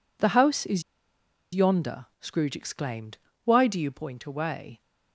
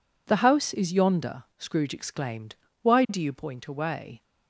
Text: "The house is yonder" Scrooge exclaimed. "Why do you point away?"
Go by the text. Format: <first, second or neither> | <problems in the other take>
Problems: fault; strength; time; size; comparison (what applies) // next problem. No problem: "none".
second | pauses between "is" and "yonder"; noticeable; at 0.8 s; 0.72 s long